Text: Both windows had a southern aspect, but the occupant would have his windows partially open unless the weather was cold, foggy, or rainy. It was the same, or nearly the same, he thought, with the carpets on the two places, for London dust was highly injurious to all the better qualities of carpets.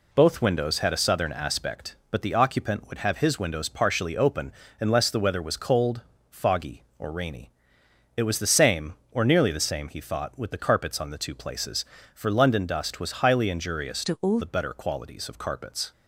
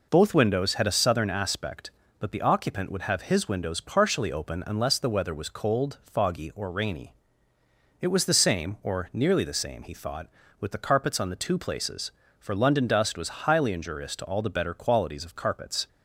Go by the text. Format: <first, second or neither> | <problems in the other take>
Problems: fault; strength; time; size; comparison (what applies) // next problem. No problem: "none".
second | pauses between "open" and "unless"; slight; at 4.5 s; 0.26 s long // changes voice from "to" to "all"; from 14.0 to 14.3 s; 0.3 s long